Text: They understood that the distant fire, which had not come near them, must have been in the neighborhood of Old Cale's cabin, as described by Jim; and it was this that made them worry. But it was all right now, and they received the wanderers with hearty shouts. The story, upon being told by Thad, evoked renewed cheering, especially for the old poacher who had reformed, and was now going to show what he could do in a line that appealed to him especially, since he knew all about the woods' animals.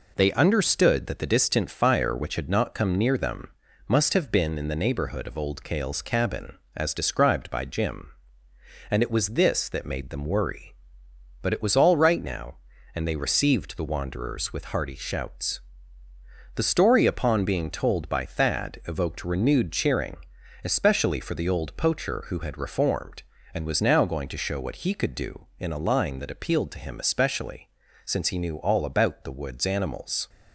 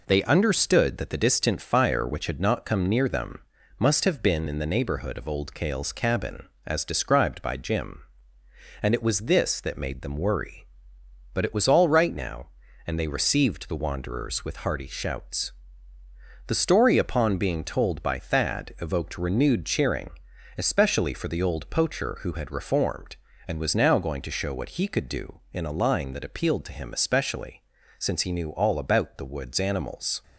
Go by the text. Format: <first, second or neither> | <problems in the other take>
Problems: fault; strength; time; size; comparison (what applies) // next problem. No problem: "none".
neither | none